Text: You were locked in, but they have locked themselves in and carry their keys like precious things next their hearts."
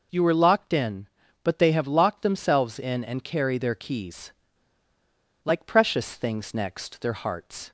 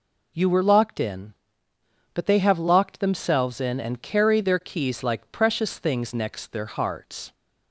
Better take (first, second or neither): second